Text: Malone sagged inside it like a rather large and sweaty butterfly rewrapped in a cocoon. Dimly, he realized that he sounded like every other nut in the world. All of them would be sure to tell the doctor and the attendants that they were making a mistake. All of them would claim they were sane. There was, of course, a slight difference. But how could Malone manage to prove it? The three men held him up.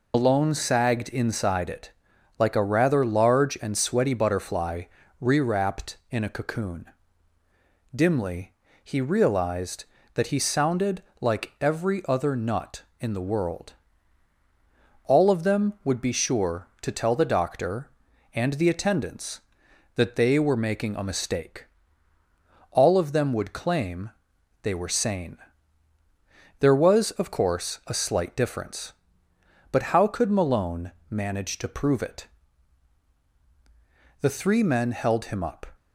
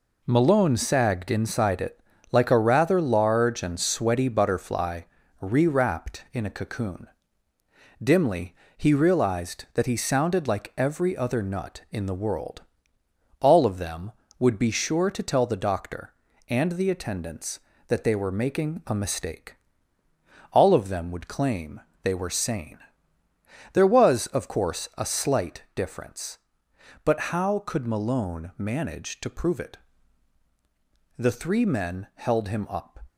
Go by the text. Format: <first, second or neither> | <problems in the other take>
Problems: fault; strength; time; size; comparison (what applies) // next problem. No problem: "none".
second | loses the start of "Malone"; at 0.1 s; 75 ms // pauses between "it" and "like"; noticeable; at 1.9 s; 0.48 s long; slight in the second // pauses between "butterfly" and "rewrapped"; at 4.8 s; 0.38 s long; also in the second // pauses between "sounded" and "like"; slight; at 11.0 s; 0.18 s long // pauses between "claim" and "they"; noticeable; at 24.1 s; 0.52 s long; slight in the second // pauses between "Malone" and "manage"; slight; at 30.9 s; 0.18 s long